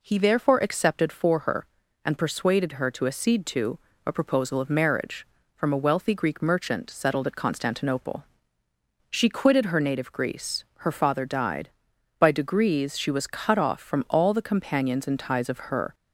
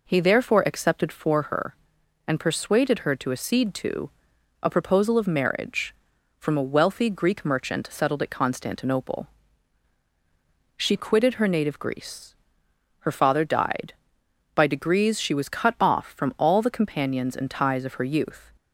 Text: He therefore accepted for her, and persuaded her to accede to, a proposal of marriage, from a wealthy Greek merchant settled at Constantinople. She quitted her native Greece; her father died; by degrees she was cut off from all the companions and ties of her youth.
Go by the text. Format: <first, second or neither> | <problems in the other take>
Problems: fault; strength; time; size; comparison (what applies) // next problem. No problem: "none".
second | stops before "youth"; at 15.9 s